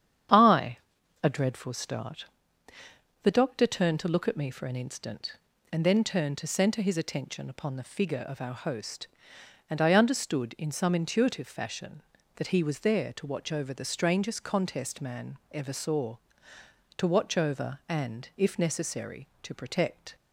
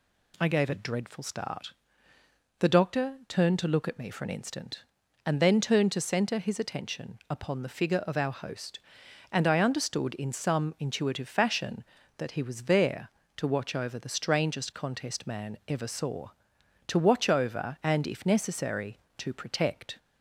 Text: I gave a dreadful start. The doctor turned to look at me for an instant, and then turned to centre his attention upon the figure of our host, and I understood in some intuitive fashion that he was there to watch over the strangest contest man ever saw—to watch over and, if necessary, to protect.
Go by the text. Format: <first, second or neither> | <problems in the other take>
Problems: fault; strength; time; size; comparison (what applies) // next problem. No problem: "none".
second | starts louder than the rest; strong; until 1.8 s; 8.5 dB // skips "gave"; at 1.0 s